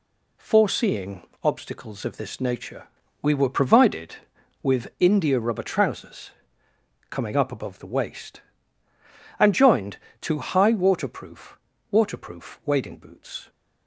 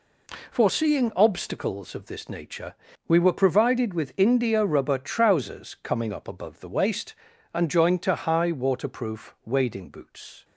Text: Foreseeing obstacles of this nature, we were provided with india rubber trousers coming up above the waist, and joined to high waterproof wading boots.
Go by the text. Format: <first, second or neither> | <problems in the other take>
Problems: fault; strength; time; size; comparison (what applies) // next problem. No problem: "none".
second | pauses between "Foreseeing" and "obstacles"; slight; at 1.2 s; 0.20 s long // pauses between "trousers" and "coming"; noticeable; at 6.3 s; 0.78 s long // says "waterproof" twice; at 11.9 s